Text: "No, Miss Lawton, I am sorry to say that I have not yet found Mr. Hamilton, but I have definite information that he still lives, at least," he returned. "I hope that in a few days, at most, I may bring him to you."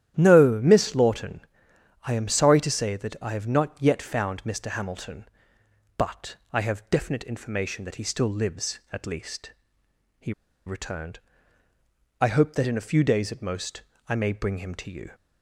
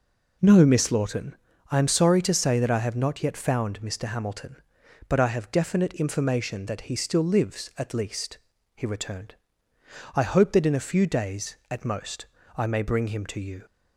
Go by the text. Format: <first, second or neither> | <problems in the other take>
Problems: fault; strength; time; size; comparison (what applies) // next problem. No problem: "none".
second | starts louder than the rest; strong; until 1.1 s; 11.5 dB // pauses between "but" and "I"; slight; at 6.3 s; 0.16 s long // pauses between "he" and "returned"; slight; at 10.3 s; 0.35 s long